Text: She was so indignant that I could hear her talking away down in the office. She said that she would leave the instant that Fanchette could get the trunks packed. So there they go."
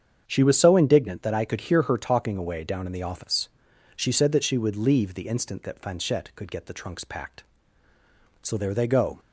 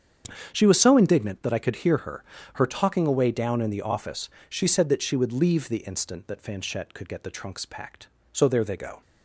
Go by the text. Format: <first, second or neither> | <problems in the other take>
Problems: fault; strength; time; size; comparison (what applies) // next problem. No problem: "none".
first | starts louder than the rest; strong; until 1.5 s; 7.5 dB; strong in the first // says "her" twice; at 2.5 s